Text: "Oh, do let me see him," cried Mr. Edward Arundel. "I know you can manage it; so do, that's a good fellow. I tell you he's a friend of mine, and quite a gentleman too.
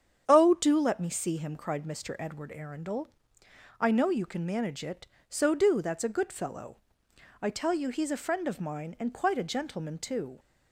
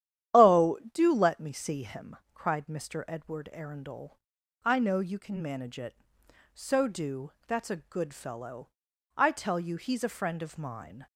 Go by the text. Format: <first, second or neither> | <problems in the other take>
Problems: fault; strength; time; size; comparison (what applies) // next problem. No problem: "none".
first | starts louder than the rest; strong; until 1.4 s; 10.5 dB; strong in the first // stops before "and quite a gentleman too"; at 11.0 s